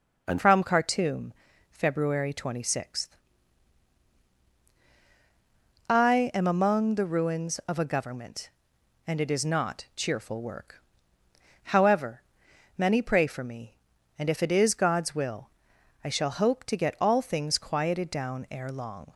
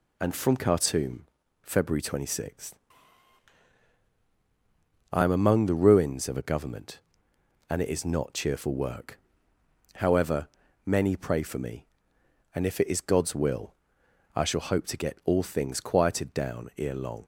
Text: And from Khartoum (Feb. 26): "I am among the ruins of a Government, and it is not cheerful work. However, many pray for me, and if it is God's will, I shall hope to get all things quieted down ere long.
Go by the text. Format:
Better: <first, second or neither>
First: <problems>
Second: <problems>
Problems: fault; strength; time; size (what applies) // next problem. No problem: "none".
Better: second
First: changes voice at "from"; from 0.3 s on; 18.8 s long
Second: none